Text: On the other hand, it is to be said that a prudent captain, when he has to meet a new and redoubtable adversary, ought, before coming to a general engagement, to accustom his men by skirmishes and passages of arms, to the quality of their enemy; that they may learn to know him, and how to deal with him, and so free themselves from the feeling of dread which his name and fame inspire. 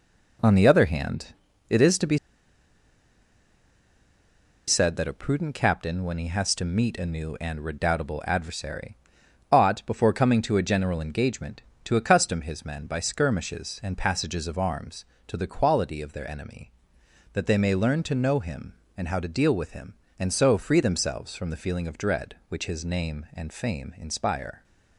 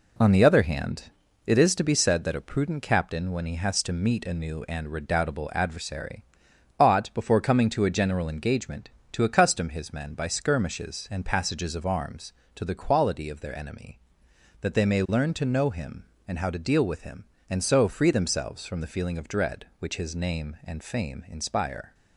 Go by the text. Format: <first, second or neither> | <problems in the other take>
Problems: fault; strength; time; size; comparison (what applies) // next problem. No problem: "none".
second | pauses between "be" and "said"; strong; at 2.1 s; 2.5 s long